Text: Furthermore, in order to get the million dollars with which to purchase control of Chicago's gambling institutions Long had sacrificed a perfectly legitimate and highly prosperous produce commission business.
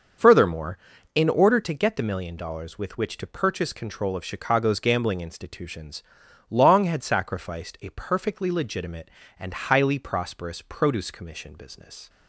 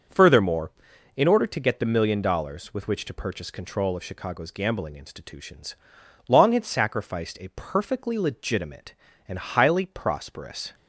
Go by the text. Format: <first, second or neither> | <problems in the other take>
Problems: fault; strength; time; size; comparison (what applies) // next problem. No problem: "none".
first | starts louder than the rest; until 1.5 s; 6.5 dB; also in the first // pauses between "institutions" and "Long"; noticeable; at 5.7 s; 0.52 s long; noticeable in the first // stops before "produce commission business"; at 10.7 s